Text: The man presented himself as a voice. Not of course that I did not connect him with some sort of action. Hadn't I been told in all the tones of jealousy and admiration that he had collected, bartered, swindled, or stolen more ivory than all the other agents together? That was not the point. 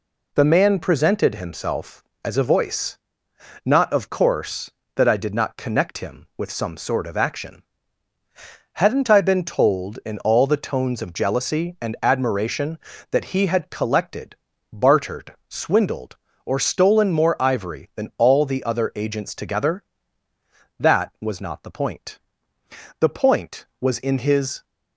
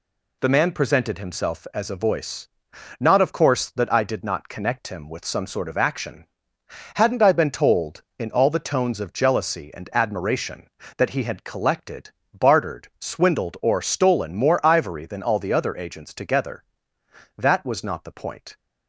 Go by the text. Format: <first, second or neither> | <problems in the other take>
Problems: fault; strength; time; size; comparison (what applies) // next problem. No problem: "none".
second | goes on to say "The point was in his"; from 22.9 s on; 1.6 s long